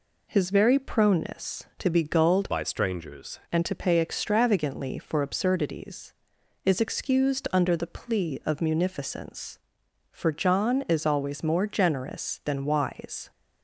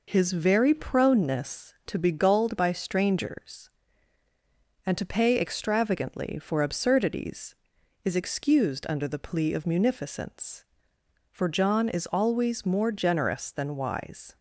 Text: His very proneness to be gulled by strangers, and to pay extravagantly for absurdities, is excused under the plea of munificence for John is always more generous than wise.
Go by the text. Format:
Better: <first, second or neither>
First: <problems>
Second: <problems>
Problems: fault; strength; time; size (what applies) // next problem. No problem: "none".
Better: second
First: changes voice from "by" to "strangers"; from 2.4 to 3.3 s; 0.9 s long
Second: none